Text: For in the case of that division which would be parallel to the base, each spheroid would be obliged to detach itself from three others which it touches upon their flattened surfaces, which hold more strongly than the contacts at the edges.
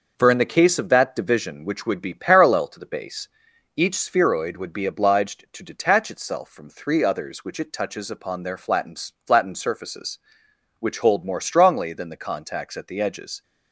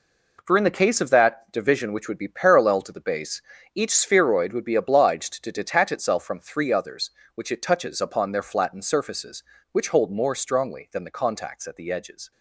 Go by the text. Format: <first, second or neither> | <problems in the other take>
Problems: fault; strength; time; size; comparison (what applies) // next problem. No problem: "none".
second | says "flattened" twice; at 9.2 s